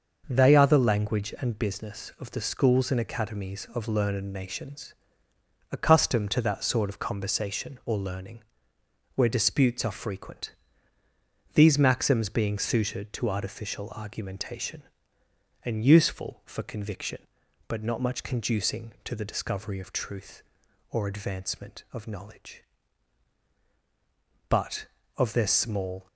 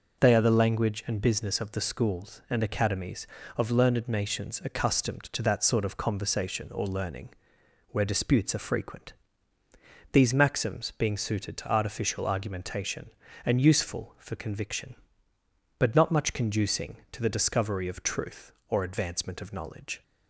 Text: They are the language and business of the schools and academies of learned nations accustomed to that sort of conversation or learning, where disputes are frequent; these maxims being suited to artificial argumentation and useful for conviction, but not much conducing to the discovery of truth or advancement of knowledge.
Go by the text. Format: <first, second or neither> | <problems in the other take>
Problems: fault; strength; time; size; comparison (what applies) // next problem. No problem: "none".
second | starts louder than the rest; until 1.2 s; 6 dB // pauses between "nations" and "accustomed"; noticeable; at 4.9 s; 0.76 s long // goes on to say "But of their small"; from 24.4 s on; 1.5 s long